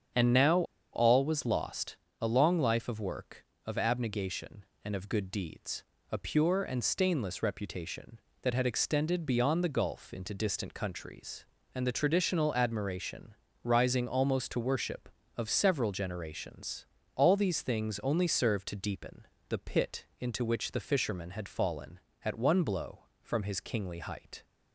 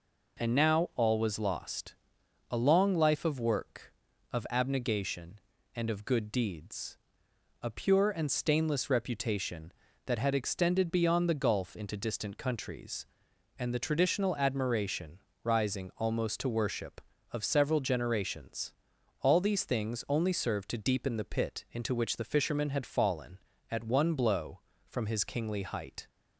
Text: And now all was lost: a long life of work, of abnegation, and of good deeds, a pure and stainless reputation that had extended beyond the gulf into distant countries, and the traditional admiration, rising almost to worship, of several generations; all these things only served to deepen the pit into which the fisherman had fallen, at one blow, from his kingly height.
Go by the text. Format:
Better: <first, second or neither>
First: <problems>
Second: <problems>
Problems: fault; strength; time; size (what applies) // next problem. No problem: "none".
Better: second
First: starts louder than the rest; strong; until 1.4 s; 7.5 dB // pauses between "now" and "all"; slight; at 0.6 s; 0.30 s long // pauses between "deepen" and "the"; slight; at 19.2 s; 0.22 s long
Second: none